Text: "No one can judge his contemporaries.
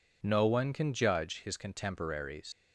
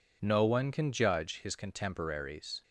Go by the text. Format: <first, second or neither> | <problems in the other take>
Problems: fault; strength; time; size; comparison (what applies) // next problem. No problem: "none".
second | leaves "contemporaries" unfinished; at 2.5 s; 115 ms